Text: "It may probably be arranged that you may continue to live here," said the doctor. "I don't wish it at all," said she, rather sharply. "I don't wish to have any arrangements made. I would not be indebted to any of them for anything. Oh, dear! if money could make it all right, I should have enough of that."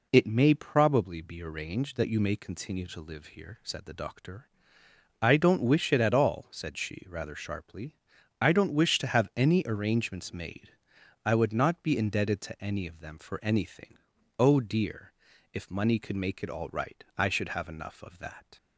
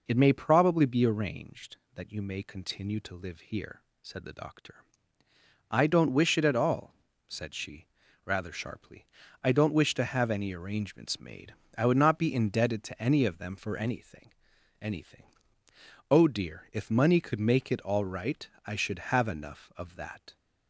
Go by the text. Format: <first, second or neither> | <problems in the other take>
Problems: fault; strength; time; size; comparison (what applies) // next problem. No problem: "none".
first | says "anything" twice; at 14.7 s